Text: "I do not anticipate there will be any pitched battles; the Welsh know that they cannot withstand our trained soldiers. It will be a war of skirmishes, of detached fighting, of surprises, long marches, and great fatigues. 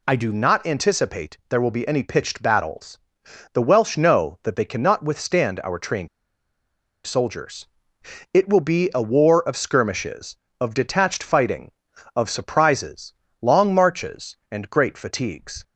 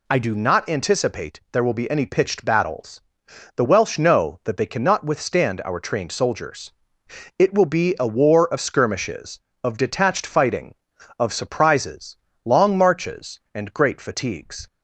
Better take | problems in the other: second | pauses between "trained" and "soldiers"; at 6.0 s; 0.98 s long

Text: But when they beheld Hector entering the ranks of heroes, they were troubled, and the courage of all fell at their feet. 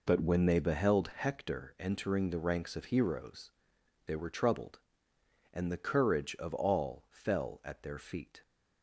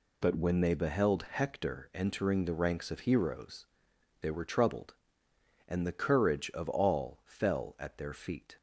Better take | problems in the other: second | starts louder than the rest; noticeable; until 1.2 s; 4 dB

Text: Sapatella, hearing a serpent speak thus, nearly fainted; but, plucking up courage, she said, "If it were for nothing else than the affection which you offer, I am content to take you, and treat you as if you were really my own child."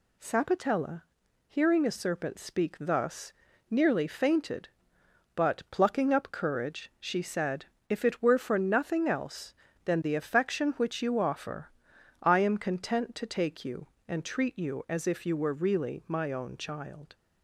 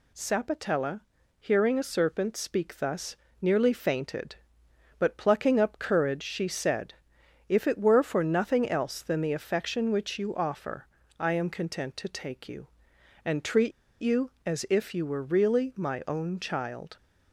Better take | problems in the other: first | pauses between "treat" and "you"; slight; at 13.7 s; 0.29 s long

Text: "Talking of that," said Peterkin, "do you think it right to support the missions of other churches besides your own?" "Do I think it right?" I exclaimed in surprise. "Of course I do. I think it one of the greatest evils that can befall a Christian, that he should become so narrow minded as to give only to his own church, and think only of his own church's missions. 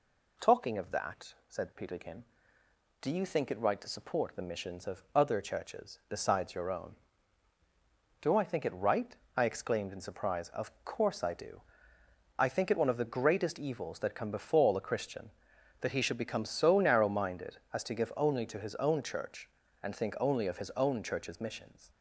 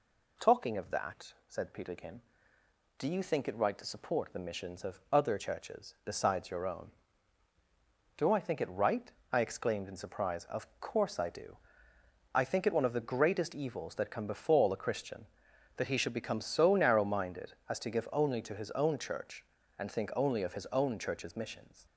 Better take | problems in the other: neither | none

